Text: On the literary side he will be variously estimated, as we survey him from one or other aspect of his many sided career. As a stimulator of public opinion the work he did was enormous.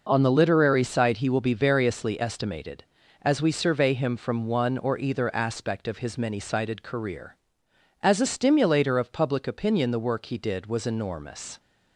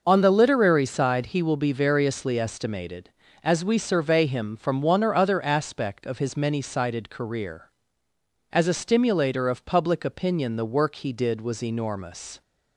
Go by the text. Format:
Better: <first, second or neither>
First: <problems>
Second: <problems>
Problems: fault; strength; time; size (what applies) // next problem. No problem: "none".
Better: second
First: says "either" for "other"; at 4.9 s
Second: none